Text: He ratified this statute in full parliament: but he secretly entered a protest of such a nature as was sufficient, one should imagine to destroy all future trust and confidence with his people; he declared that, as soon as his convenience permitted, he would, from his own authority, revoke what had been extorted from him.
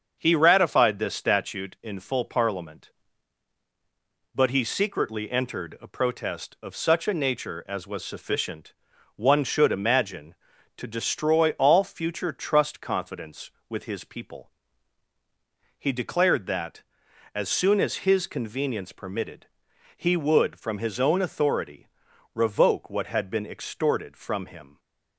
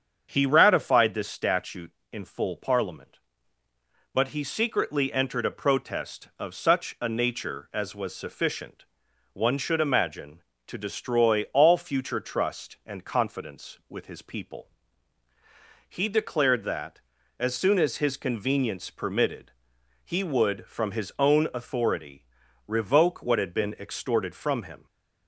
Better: second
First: starts louder than the rest; until 1.1 s; 6.5 dB // skips "and"; at 12.8 s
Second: starts louder than the rest; strong; until 1.3 s; 7 dB

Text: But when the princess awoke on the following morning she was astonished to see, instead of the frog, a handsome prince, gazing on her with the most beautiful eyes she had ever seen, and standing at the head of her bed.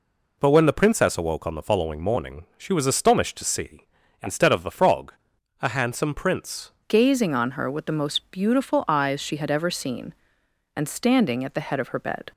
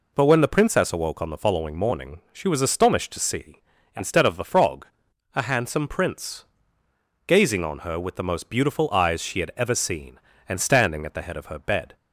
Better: second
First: changes voice at "gazing"; from 6.8 s on; 5.5 s long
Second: none

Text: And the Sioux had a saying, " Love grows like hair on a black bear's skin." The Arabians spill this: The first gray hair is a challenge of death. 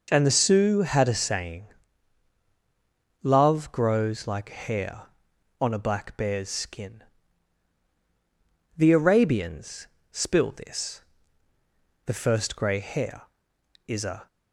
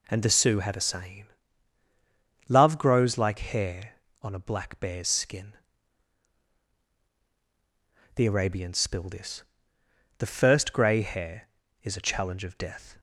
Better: second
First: pauses between "Arabians" and "spill"; slight; at 9.8 s; 0.26 s long // stops before "challenge of death"; at 14.2 s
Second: none

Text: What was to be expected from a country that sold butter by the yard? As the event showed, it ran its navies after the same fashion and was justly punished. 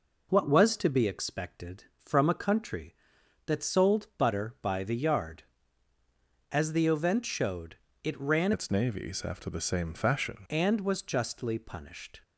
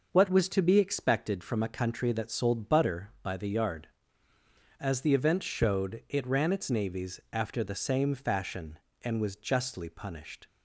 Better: second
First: changes voice from "its" to "fashion"; from 8.5 to 10.4 s; 1.9 s long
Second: none

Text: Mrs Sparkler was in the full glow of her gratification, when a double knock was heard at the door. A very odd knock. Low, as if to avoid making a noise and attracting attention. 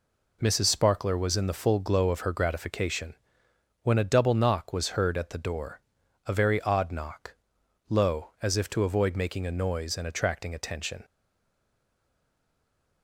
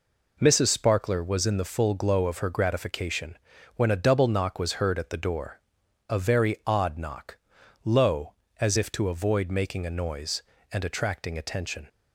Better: second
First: stays silent after the last word; noticeable; from 11.0 s on; 2.0 s long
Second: none

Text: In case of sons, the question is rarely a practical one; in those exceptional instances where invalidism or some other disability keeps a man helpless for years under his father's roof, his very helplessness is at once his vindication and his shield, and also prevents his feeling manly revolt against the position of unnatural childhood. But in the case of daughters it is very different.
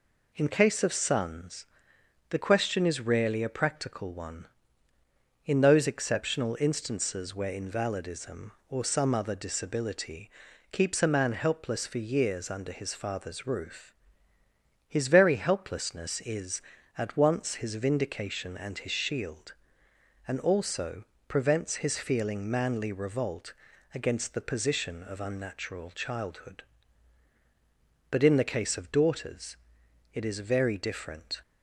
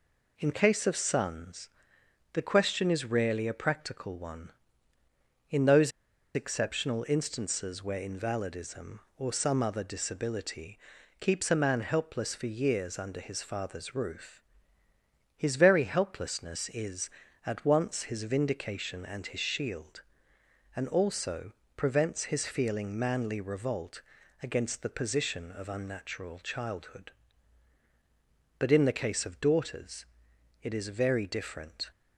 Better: first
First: pauses between "disability" and "keeps"; at 10.2 s; 0.42 s long // pauses between "also" and "prevents"; slight; at 21.0 s; 0.24 s long // pauses between "revolt" and "against"; at 23.5 s; 0.42 s long // pauses between "daughters" and "it"; noticeable; at 29.5 s; 0.56 s long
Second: pauses between "those" and "exceptional"; at 5.9 s; 0.44 s long // pauses between "disability" and "keeps"; at 10.7 s; 0.42 s long // pauses between "also" and "prevents"; slight; at 21.5 s; 0.24 s long // pauses between "revolt" and "against"; at 23.9 s; 0.42 s long // pauses between "daughters" and "it"; noticeable; at 30.0 s; 0.56 s long

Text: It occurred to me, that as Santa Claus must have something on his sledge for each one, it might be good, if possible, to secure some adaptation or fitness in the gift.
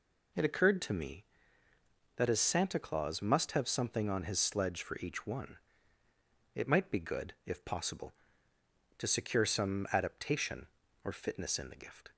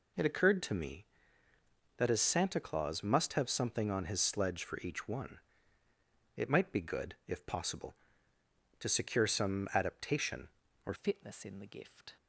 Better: first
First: none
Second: changes voice at "fitness"; from 10.9 s on; 1.2 s long

